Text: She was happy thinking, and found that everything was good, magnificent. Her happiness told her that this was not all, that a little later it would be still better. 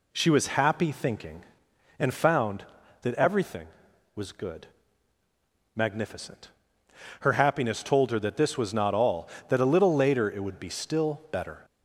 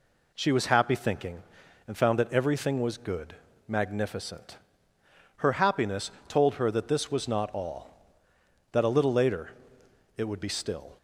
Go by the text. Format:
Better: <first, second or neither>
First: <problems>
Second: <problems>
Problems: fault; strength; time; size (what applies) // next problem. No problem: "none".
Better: first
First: none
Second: pauses between "happiness" and "told"; slight; at 6.0 s; 0.18 s long // pauses between "later" and "it"; noticeable; at 9.4 s; 0.64 s long // stops before "better"; at 10.9 s